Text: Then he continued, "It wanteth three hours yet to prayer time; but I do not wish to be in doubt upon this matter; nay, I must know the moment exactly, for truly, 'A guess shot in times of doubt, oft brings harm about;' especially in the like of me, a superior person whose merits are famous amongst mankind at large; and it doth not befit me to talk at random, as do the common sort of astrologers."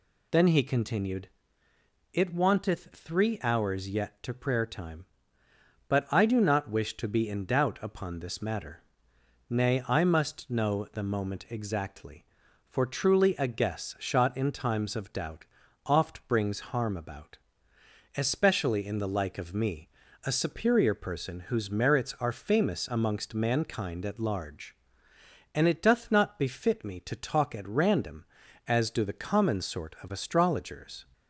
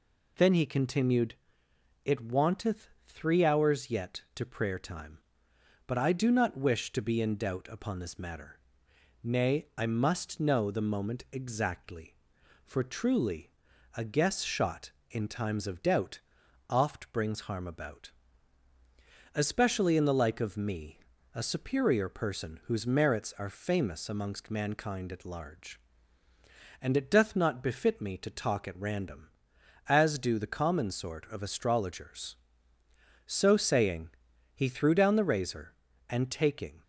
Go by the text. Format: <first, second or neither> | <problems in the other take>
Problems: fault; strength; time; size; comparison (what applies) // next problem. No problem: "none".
first | pauses between "wanteth" and "three"; slight; at 2.8 s; 0.18 s long // goes on to say "So saying he threw down the razor and taking"; strong; from 33.2 s on; 3.5 s long